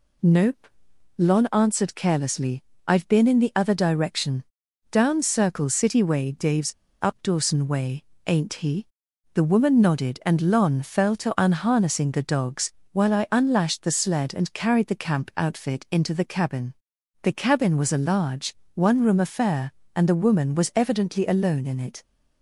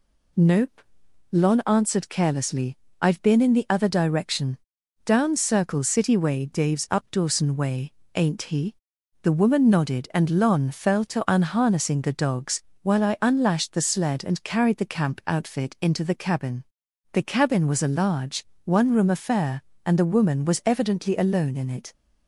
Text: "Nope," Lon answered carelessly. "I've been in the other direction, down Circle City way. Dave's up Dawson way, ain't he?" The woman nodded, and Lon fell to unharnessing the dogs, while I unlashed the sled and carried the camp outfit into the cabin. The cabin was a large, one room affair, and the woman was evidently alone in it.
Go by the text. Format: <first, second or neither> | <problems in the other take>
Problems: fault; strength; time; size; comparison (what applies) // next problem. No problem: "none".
second | pauses between "Dave's" and "up"; slight; at 6.7 s; 0.29 s long